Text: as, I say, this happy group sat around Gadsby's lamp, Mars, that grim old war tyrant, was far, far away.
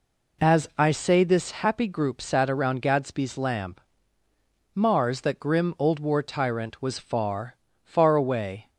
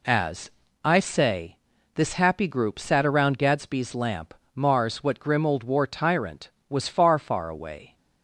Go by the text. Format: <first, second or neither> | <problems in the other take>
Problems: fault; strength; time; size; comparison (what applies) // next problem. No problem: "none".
first | says "what" for "that"; at 5.0 s